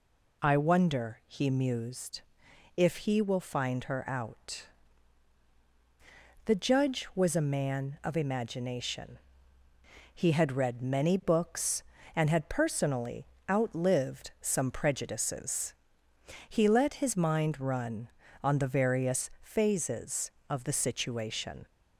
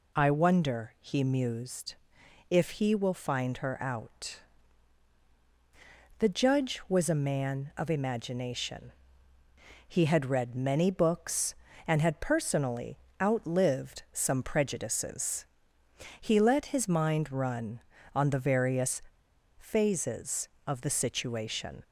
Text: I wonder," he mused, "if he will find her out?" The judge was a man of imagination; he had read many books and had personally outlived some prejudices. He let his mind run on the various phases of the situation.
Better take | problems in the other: first | pauses between "personally" and "outlived"; slight; at 12.9 s; 0.22 s long; slight in the first // pauses between "various" and "phases"; noticeable; at 19.0 s; 0.57 s long

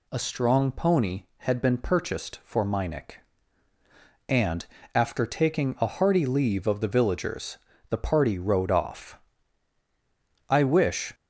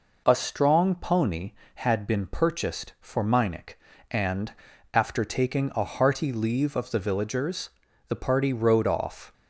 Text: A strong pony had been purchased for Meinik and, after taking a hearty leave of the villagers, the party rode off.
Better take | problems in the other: second | goes on to say "I wish"; noticeable; from 10.4 s on; 0.64 s long

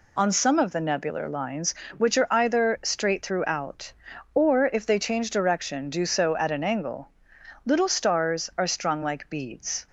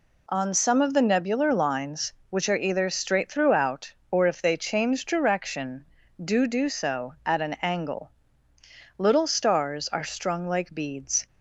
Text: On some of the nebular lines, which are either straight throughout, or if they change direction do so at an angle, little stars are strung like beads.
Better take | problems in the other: first | says "do" twice; at 6.4 s

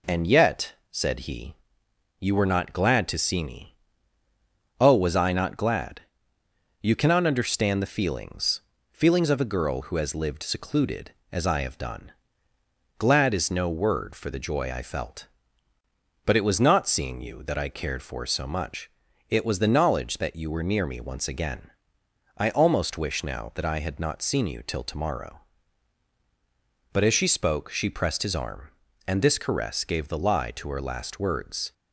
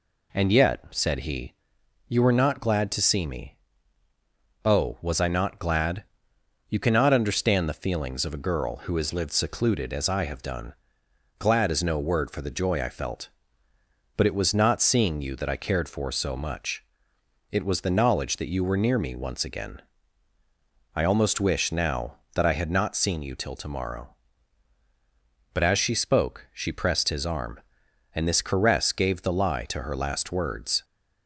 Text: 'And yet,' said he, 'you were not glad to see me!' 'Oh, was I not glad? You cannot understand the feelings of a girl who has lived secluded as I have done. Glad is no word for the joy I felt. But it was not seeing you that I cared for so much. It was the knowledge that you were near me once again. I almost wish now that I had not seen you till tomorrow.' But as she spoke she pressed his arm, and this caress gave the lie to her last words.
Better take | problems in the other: second | says "feelings" twice; at 8.9 s

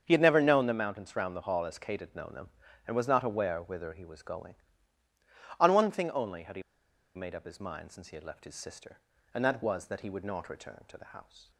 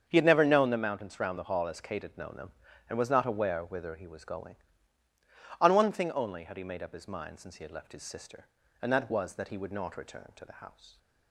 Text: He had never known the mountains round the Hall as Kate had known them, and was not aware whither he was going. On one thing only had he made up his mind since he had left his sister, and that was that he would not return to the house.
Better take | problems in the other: second | starts louder than the rest; strong; until 1.0 s; 7 dB; strong in the second // pauses between "he" and "made"; noticeable; at 6.6 s; 0.53 s long

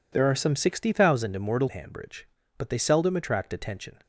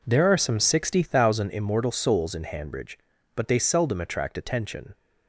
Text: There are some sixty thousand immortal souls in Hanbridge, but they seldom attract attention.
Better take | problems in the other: second | skips "souls in"; at 1.6 s

